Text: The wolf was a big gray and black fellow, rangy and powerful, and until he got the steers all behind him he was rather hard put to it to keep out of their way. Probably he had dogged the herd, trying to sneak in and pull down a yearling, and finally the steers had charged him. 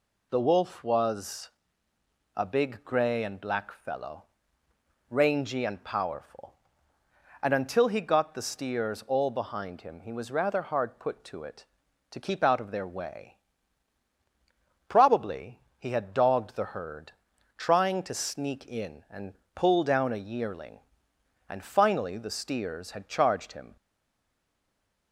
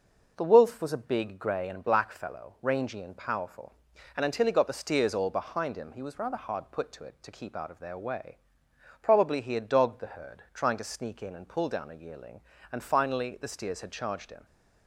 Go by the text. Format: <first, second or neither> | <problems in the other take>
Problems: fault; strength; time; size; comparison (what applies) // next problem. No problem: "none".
second | pauses between "was" and "a"; noticeable; at 1.4 s; 0.86 s long // pauses between "Probably" and "he"; slight; at 15.5 s; 0.18 s long // pauses between "and" and "pull"; slight; at 19.3 s; 0.20 s long // stays silent after the last word; noticeable; from 23.7 s on; 1.4 s long